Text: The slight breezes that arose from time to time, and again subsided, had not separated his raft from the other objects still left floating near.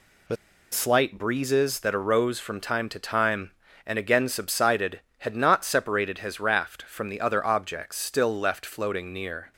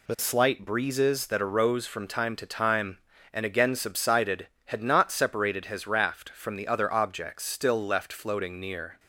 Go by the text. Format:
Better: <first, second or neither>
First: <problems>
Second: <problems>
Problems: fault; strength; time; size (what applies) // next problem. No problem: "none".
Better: second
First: pauses between "The" and "slight"; at 0.3 s; 0.36 s long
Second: none